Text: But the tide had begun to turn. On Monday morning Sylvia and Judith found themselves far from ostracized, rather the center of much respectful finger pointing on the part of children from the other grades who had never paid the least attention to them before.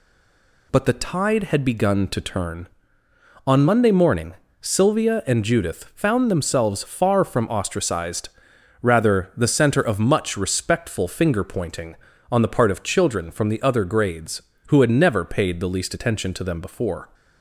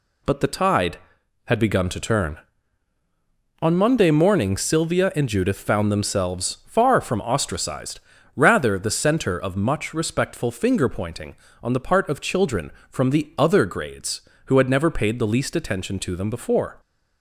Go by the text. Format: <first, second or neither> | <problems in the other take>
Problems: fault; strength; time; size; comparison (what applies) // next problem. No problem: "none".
second | stays silent before the first word; slight; until 0.7 s; 0.7 s long // pauses between "morning" and "Sylvia"; slight; at 4.3 s; 0.26 s long